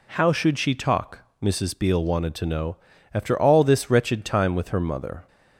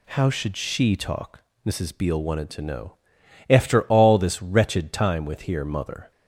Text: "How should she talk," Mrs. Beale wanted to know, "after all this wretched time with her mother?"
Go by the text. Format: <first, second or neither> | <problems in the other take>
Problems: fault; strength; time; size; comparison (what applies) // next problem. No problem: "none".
first | says "here" for "her"; at 5.4 s